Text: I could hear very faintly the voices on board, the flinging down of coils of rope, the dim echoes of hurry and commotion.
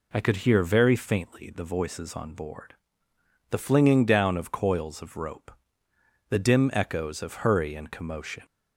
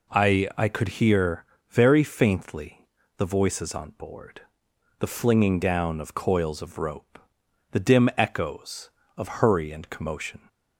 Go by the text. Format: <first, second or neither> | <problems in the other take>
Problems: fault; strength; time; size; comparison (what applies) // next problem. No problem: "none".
first | says "I" twice; at 0.5 s // pauses between "hear" and "very"; slight; at 1.4 s; 0.26 s long // pauses between "faintly" and "the"; slight; at 2.8 s; 0.30 s long